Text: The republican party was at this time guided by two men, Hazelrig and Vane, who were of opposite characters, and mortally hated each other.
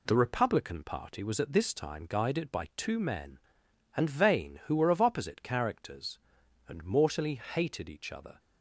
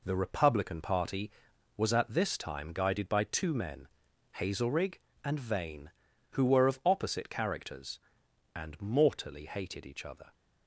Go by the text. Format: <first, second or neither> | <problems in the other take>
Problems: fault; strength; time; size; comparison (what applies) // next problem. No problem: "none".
second | skips "Hazelrig"; at 3.6 s